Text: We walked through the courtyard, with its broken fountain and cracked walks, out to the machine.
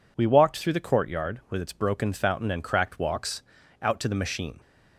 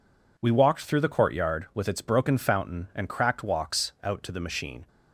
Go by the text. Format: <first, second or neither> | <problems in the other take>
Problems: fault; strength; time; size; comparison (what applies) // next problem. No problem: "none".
neither | none